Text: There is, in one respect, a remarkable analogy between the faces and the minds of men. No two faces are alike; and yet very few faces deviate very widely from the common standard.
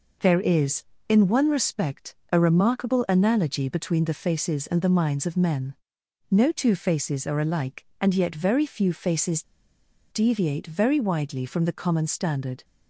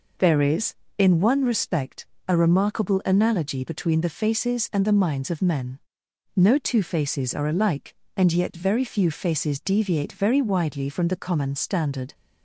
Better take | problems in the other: second | pauses between "faces" and "deviate"; noticeable; at 9.4 s; 0.67 s long

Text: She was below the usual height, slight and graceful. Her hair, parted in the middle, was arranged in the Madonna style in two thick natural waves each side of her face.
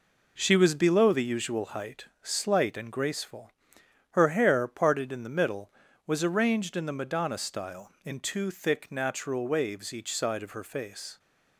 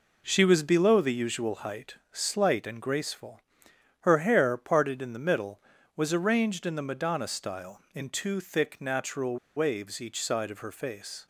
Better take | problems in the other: first | pauses between "natural" and "waves"; slight; at 9.3 s; 0.19 s long

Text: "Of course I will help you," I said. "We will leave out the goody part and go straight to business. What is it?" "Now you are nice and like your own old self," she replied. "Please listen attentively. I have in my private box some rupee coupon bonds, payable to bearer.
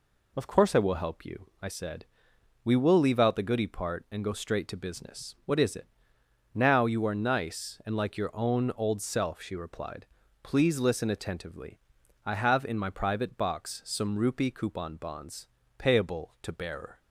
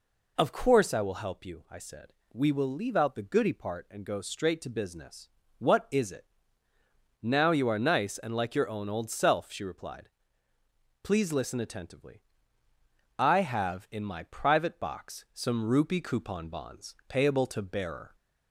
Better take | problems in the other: neither | none

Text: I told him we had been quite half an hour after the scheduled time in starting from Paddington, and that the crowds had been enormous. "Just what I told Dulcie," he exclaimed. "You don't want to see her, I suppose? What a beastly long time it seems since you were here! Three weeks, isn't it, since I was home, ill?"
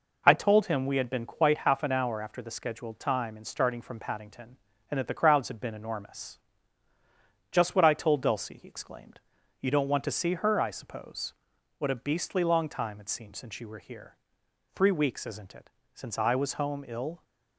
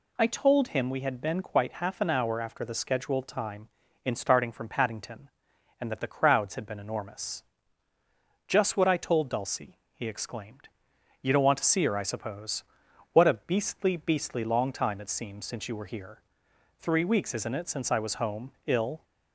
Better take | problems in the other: first | says "beastly" twice; at 13.9 s

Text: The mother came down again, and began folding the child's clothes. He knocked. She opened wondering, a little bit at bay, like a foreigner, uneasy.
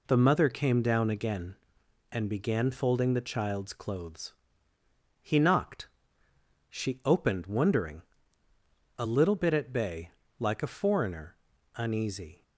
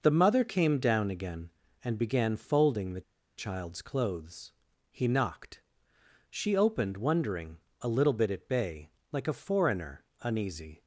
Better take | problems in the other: first | pauses between "the" and "child's"; slight; at 3.0 s; 0.35 s long

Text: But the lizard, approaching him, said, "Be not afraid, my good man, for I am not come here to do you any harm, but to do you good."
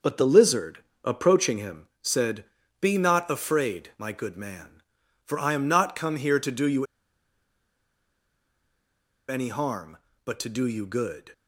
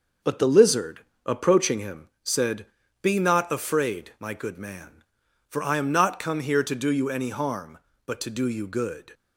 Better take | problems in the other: second | pauses between "you" and "any"; strong; at 6.8 s; 2.4 s long

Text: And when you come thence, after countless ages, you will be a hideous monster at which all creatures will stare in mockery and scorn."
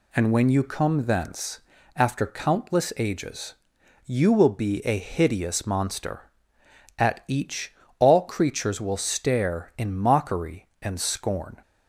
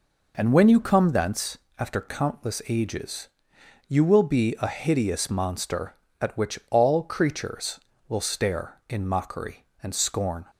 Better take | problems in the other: second | says "each" for "which"; at 7.2 s

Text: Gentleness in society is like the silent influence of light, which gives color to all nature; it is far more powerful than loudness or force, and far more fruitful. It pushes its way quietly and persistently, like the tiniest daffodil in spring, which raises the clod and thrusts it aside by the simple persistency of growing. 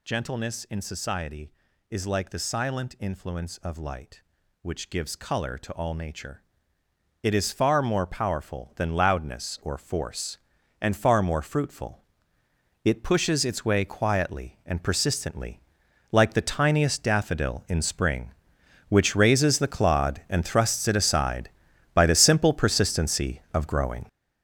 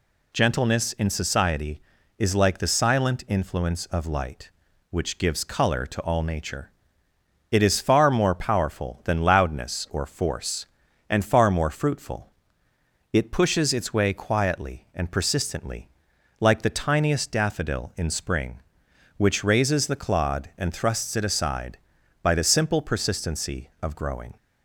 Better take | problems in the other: second | gets louder; strong; throughout; 9.5 dB

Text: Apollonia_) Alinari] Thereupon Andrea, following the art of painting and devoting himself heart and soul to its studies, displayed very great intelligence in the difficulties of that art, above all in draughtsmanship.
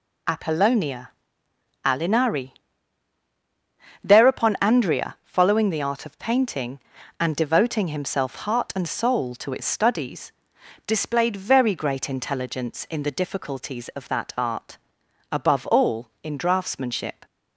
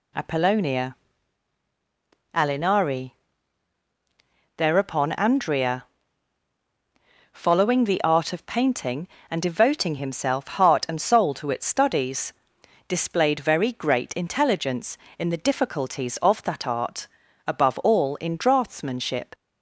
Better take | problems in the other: neither | pauses between "Alinari" and "Thereupon"; strong; the same in both

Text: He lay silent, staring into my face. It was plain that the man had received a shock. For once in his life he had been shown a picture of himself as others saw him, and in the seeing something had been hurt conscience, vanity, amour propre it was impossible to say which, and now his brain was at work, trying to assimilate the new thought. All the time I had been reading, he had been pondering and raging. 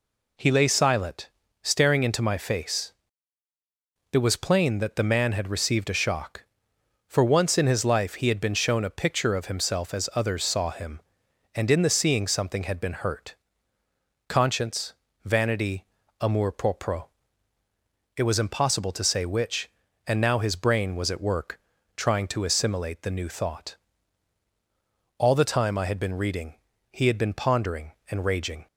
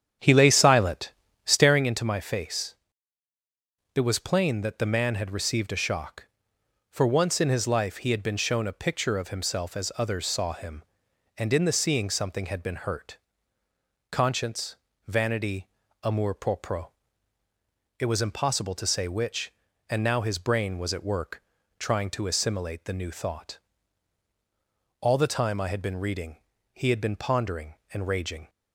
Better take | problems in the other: first | starts louder than the rest; strong; until 1.9 s; 9 dB // pauses between "hurt" and "conscience"; noticeable; at 13.1 s; 0.94 s long; noticeable in the first // pauses between "propre" and "it"; at 16.8 s; 1.1 s long; also in the first

